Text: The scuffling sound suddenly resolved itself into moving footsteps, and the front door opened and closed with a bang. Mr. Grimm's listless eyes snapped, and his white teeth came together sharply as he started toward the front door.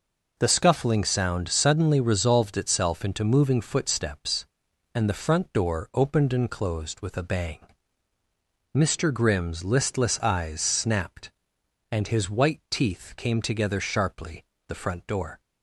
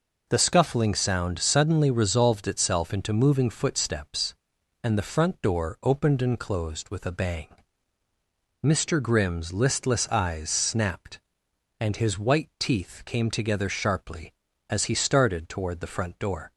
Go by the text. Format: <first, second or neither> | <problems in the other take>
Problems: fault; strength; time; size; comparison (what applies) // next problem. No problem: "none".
second | skips "as he started toward"; at 14.5 s